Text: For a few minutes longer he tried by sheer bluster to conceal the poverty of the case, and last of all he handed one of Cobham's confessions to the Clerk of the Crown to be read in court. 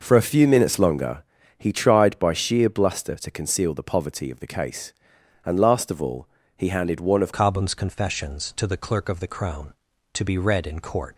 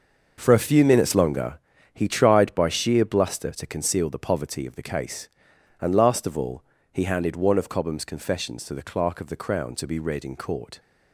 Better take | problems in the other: second | pauses between "longer" and "he"; at 1.2 s; 0.38 s long; also in the second // pauses between "all" and "he"; slight; at 6.2 s; 0.30 s long; slight in the second // changes voice at "Cobham's"; from 7.3 s on; 3.8 s long

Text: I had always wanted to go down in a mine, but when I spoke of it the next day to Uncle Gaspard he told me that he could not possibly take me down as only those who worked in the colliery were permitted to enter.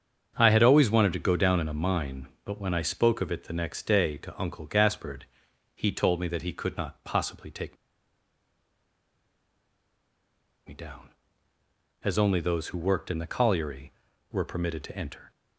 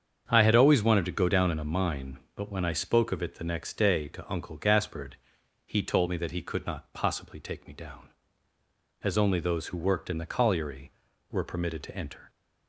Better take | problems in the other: second | starts louder than the rest; strong; until 1.3 s; 7.5 dB; strong in the second // pauses between "Gaspard" and "he"; noticeable; at 5.2 s; 0.50 s long; noticeable in the second // pauses between "take" and "me"; strong; at 7.7 s; 2.9 s long

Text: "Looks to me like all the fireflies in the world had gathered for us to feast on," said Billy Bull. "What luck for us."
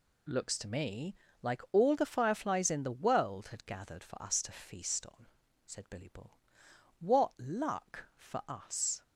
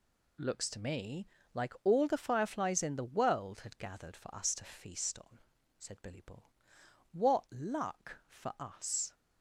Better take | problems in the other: neither | pauses between "me" and "like"; slight; the same in both

